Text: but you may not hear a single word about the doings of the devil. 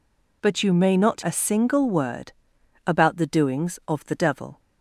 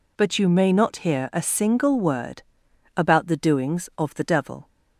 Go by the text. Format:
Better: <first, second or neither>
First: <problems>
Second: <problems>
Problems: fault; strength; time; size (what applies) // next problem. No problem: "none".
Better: second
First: skips "hear"; at 1.2 s // pauses between "word" and "about"; noticeable; at 2.3 s; 0.52 s long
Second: pauses between "word" and "about"; noticeable; at 2.4 s; 0.52 s long